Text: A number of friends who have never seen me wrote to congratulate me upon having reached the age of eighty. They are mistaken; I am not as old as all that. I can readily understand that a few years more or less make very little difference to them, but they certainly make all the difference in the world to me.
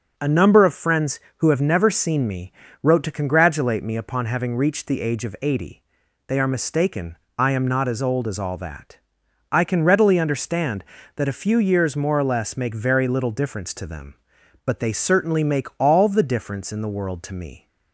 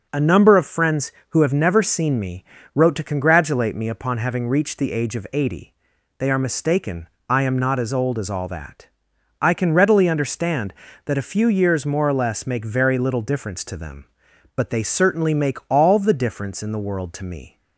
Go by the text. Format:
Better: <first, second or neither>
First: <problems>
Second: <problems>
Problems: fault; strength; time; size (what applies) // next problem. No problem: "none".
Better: neither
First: pauses between "me" and "wrote"; slight; at 2.5 s; 0.32 s long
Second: pauses between "me" and "wrote"; slight; at 2.4 s; 0.32 s long